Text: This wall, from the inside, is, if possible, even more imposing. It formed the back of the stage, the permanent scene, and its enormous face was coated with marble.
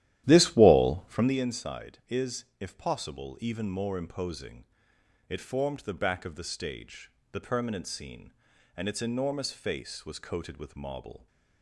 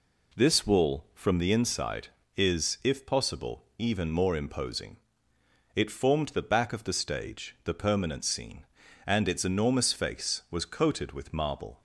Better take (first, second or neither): second